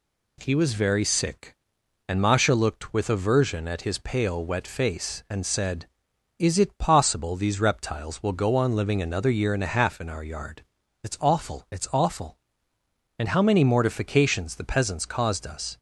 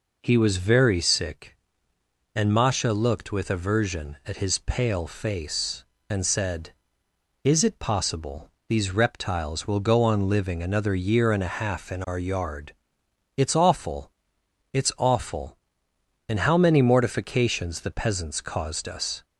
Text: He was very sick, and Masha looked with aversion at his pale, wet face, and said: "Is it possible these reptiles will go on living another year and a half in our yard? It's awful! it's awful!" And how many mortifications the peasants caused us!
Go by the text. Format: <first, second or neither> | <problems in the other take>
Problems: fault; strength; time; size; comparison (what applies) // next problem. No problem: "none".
first | skips "wet"; at 5.0 s // pauses between "possible" and "these"; slight; at 8.5 s; 0.18 s long